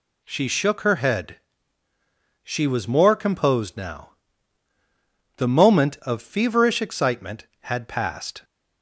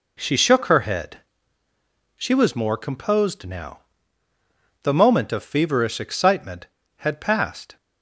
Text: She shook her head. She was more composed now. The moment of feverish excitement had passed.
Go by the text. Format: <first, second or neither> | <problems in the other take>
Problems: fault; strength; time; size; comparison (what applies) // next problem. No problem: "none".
neither | none